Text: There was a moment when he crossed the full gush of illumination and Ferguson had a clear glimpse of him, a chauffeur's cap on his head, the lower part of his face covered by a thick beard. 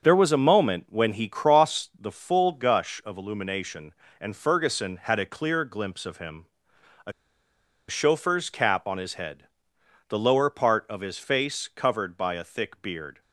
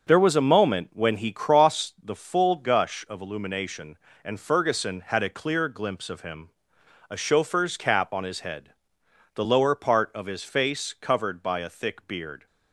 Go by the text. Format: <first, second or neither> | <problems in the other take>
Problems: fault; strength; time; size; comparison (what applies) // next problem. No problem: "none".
second | starts louder than the rest; noticeable; until 1.0 s; 6 dB; noticeable in the second // pauses between "a" and "chauffeur's"; noticeable; at 7.1 s; 0.78 s long